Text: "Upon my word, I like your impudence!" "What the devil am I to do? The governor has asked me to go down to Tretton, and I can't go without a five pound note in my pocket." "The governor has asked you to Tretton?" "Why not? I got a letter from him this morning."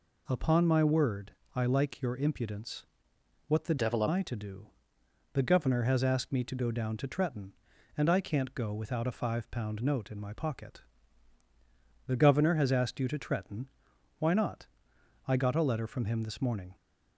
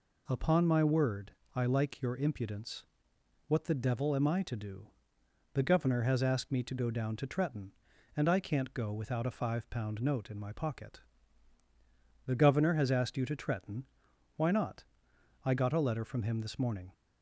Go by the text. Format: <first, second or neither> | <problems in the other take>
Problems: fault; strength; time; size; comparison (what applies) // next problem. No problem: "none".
second | changes voice from "devil" to "am"; from 3.7 to 4.0 s; 0.3 s long